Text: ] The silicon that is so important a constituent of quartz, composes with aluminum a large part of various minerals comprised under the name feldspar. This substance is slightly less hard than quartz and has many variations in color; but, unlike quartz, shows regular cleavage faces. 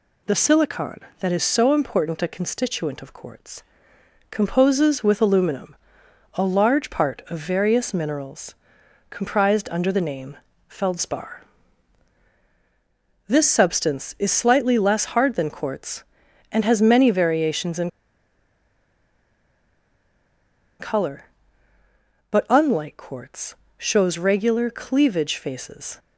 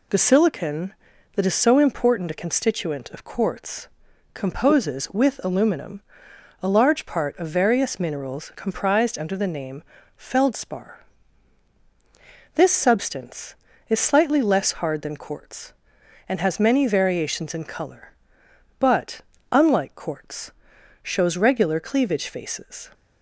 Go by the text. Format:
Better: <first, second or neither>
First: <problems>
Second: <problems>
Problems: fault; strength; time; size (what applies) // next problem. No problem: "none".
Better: second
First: pauses between "aluminum" and "a"; noticeable; at 5.7 s; 0.60 s long // pauses between "minerals" and "comprised"; noticeable; at 8.5 s; 0.54 s long // pauses between "name" and "feldspar"; slight; at 10.3 s; 0.32 s long // pauses between "in" and "color"; strong; at 17.8 s; 2.9 s long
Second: pauses between "aluminum" and "a"; noticeable; at 5.9 s; 0.62 s long // pauses between "name" and "feldspar"; slight; at 9.8 s; 0.34 s long